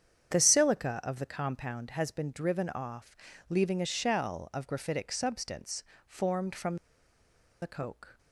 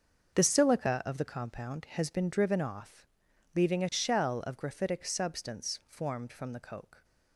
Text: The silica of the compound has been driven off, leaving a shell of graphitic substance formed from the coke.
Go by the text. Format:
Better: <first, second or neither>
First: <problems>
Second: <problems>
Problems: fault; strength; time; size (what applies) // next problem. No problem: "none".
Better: second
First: starts louder than the rest; strong; until 1.3 s; 8.5 dB // pauses between "substance" and "formed"; slight; at 5.8 s; 0.24 s long // pauses between "from" and "the"; noticeable; at 6.7 s; 0.85 s long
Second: starts louder than the rest; until 1.3 s; 6.5 dB